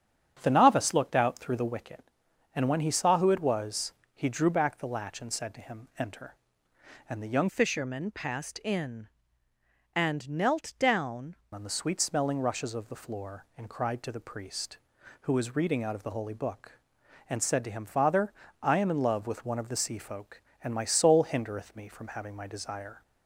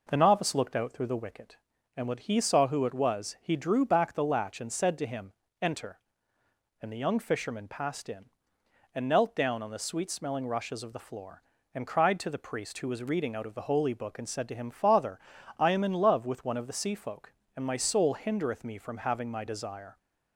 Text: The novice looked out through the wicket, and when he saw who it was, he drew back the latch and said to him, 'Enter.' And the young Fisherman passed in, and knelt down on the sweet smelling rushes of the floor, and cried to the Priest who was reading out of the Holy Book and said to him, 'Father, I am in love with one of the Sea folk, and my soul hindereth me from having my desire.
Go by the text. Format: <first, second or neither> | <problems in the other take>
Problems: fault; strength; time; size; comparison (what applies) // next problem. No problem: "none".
second | starts louder than the rest; strong; until 1.4 s; 8 dB // changes voice from "Fisherman" to "down"; from 7.4 to 11.3 s; 3.9 s long